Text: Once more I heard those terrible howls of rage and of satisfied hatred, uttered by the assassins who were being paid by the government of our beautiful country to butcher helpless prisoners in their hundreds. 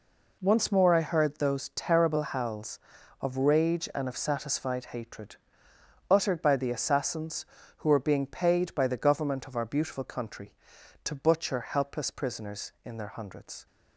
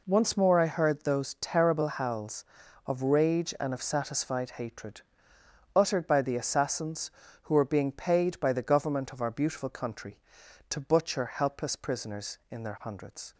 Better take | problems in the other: neither | none

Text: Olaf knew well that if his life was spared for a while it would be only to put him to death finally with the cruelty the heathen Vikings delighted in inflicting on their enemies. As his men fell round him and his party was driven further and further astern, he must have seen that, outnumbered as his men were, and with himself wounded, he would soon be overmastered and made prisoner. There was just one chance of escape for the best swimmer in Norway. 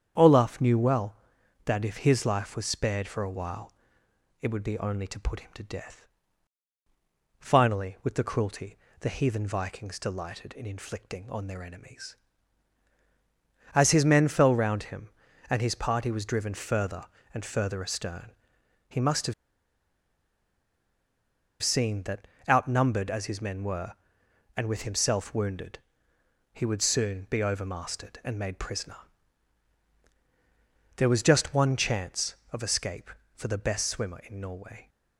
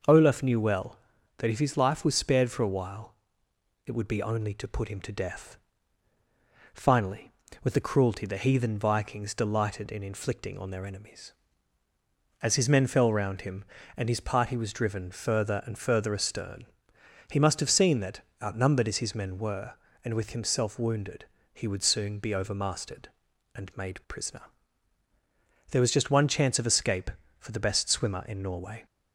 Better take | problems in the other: second | starts louder than the rest; strong; until 1.6 s; 8.5 dB // pauses between "while" and "it"; noticeable; at 3.7 s; 0.68 s long; noticeable in the second // pauses between "death" and "finally"; strong; at 6.0 s; 1.3 s long; also in the second // pauses between "cruelty" and "the"; slight; at 8.7 s; 0.24 s long // pauses between "have" and "seen"; strong; at 19.3 s; 2.2 s long

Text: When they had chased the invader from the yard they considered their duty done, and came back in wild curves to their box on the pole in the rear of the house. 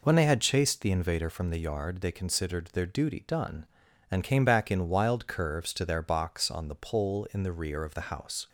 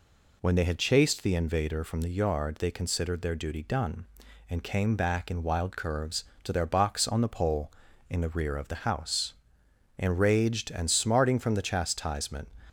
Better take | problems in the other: first | goes on to say "Enraged and smarting from the chastisement"; strong; from 9.9 s on; 2.5 s long

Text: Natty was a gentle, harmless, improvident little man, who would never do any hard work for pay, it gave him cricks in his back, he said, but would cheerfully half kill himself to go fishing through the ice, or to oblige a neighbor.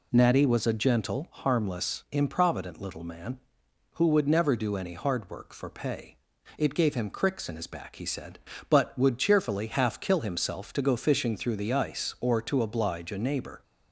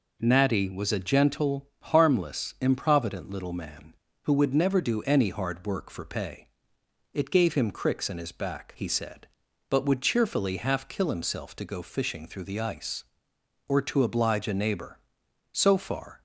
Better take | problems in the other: first | goes on to say "So far"; noticeable; from 15.5 s on; 0.70 s long

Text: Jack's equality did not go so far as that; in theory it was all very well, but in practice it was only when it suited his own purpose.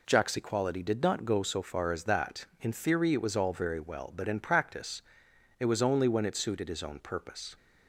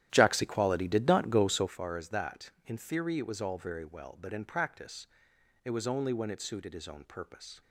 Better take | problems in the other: first | starts louder than the rest; strong; until 1.8 s; 11.5 dB // pauses between "practice" and "it"; noticeable; at 5.0 s; 0.56 s long; noticeable in the first

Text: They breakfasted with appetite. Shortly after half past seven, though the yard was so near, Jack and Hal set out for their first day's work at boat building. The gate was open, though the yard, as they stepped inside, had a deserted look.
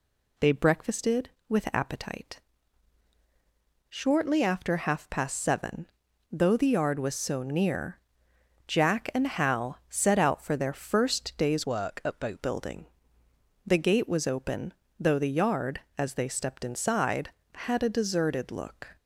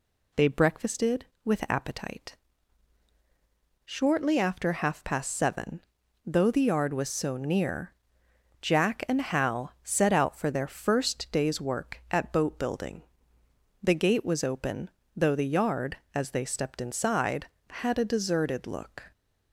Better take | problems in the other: second | changes voice from "work" to "boat"; from 11.6 to 12.4 s; 0.8 s long

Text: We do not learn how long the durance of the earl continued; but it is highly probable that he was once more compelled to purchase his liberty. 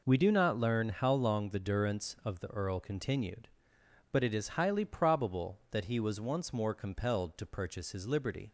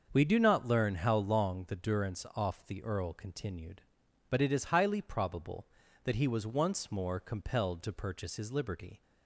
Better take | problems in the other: first | starts louder than the rest; until 1.1 s; 6.5 dB // says "off" for "of"; at 2.3 s

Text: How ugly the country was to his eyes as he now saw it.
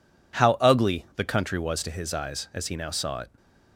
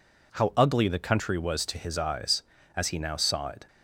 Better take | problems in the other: neither | none

